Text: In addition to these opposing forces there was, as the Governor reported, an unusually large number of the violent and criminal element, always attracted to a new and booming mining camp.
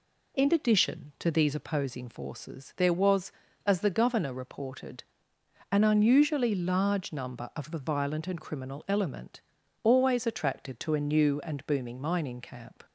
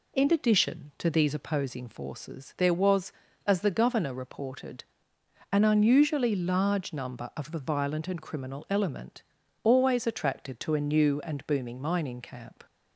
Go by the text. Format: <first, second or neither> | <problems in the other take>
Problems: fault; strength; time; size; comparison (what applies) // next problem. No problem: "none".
neither | none